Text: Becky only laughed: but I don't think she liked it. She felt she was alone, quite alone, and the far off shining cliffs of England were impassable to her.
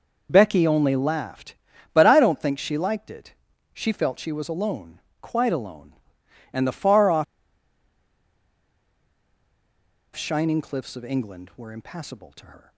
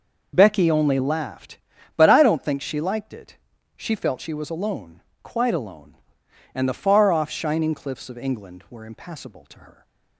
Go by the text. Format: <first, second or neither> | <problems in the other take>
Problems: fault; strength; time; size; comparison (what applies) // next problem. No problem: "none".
second | pauses between "off" and "shining"; strong; at 7.2 s; 2.9 s long